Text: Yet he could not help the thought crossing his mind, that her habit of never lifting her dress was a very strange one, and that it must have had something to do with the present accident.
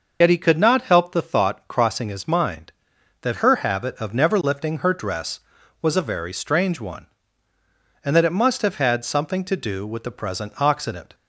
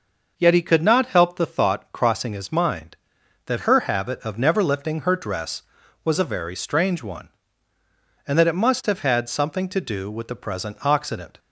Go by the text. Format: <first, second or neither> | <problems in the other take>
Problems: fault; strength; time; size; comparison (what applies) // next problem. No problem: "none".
second | loses the start of "Yet"; at 0.2 s; 75 ms // starts louder than the rest; noticeable; until 1.2 s; 6 dB